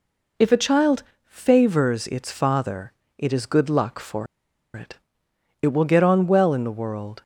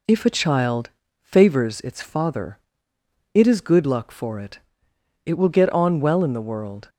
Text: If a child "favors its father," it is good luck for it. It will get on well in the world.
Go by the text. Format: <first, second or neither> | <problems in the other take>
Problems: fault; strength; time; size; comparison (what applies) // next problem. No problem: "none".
second | pauses between "child" and "favors"; slight; at 1.0 s; 0.22 s long; slight in the second // pauses between "for" and "it"; noticeable; at 4.2 s; 0.50 s long